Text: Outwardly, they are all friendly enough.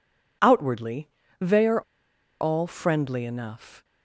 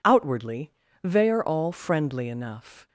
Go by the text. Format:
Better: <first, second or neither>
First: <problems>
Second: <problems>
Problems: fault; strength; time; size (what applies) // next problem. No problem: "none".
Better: second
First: pauses between "are" and "all"; noticeable; at 1.8 s; 0.59 s long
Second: none